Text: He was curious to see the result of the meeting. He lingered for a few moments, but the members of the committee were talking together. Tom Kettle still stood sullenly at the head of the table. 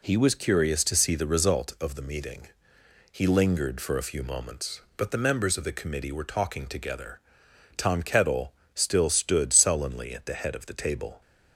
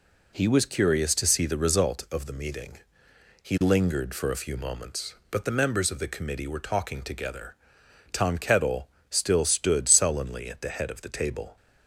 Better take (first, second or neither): neither